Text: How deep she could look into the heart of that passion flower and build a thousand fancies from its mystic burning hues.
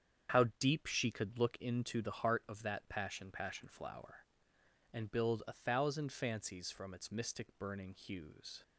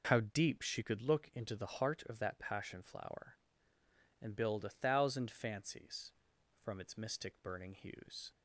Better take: second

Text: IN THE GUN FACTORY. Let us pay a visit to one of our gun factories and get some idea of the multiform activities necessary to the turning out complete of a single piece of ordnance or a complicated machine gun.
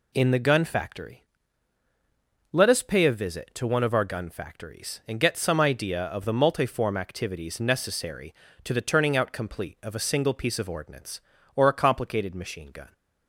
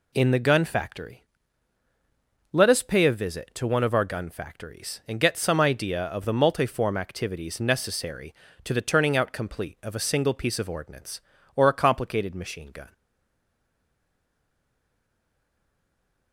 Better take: first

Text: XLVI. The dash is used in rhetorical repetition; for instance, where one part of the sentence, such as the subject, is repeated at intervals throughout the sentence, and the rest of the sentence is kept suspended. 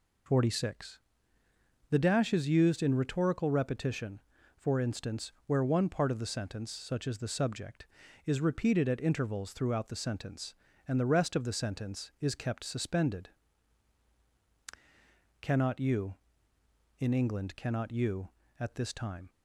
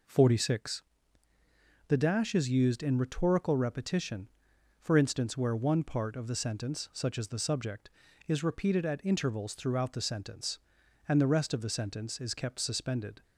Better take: second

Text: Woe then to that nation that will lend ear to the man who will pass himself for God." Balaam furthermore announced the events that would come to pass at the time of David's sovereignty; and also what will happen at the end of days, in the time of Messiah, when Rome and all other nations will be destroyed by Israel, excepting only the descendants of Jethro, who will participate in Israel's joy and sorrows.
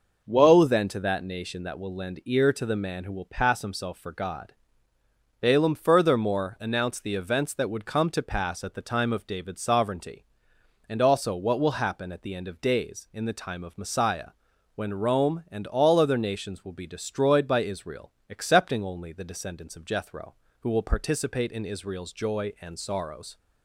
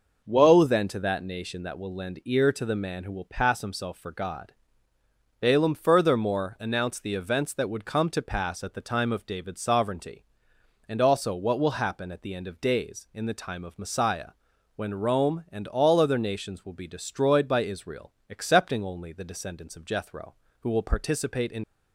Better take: first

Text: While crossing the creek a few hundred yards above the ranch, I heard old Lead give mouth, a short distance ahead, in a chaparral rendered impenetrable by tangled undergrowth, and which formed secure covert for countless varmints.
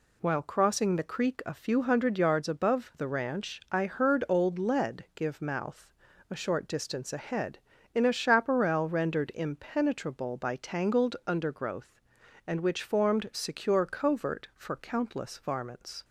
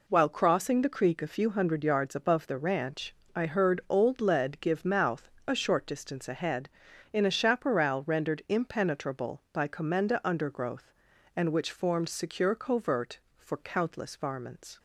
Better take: first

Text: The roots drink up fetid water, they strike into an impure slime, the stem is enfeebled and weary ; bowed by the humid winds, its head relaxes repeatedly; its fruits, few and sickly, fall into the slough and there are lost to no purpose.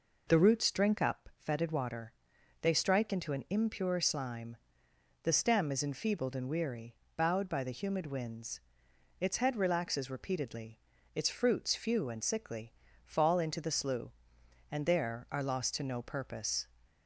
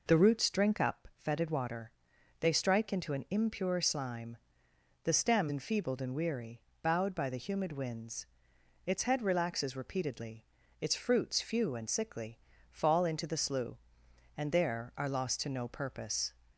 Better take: first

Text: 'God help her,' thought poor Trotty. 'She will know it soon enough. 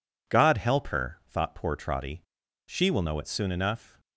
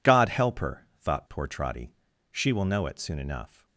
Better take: neither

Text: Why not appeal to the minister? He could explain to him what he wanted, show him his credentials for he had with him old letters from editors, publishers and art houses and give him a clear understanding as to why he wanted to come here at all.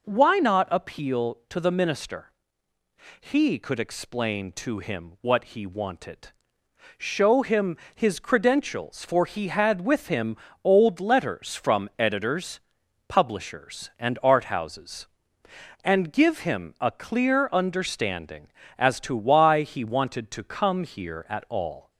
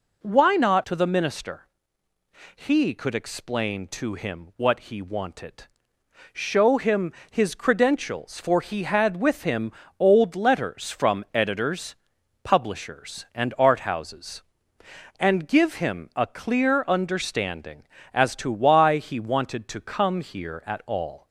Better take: first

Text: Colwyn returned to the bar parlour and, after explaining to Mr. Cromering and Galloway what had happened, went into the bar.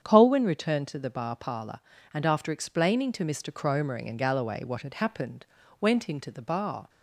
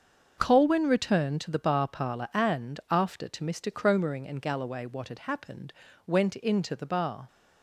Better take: first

